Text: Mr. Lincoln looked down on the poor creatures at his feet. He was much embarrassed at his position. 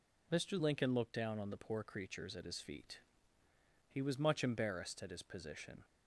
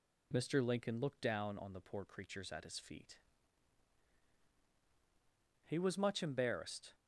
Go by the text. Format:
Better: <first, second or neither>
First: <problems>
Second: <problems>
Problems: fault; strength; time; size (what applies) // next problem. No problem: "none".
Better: first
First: none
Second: stops before "at his position"; at 6.9 s